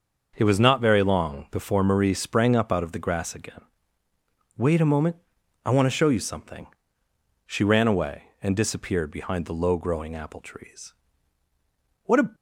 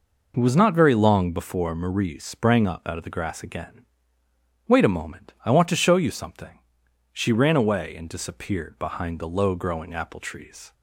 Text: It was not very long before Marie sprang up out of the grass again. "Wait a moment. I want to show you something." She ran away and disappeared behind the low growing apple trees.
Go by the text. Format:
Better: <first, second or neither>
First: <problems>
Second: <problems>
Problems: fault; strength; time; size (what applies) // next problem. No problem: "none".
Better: second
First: starts louder than the rest; until 1.3 s; 6 dB // goes on to say "What a"; slight; from 12.0 s on; 0.32 s long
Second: none